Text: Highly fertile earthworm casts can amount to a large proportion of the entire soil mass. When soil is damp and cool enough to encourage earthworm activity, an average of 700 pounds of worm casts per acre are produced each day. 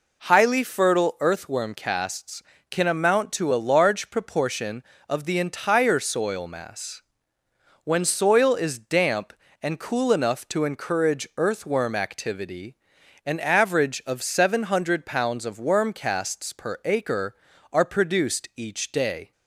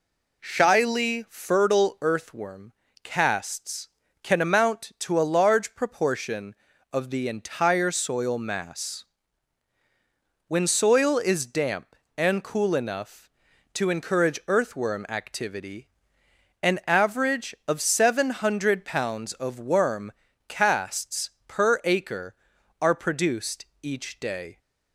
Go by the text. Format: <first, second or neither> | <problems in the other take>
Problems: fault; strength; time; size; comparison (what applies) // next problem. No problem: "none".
first | says "Shyly" for "Highly"; at 0.4 s // pauses between "earthworm" and "casts"; slight; at 2.7 s; 0.30 s long // pauses between "worm" and "casts"; slight; at 20.1 s; 0.34 s long // pauses between "casts" and "per"; slight; at 21.3 s; 0.18 s long // pauses between "produced" and "each"; slight; at 23.6 s; 0.18 s long